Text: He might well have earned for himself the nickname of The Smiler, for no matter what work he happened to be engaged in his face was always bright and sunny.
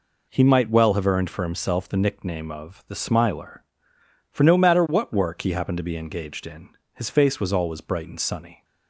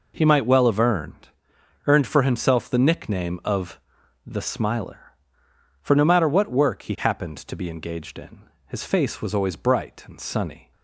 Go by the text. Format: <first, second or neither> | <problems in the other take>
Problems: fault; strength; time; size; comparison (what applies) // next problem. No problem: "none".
first | says "earned" twice; at 1.8 s // pauses between "of" and "The"; noticeable; at 3.7 s; 0.46 s long // pauses between "in" and "his"; slight; at 8.4 s; 0.24 s long; slight in the first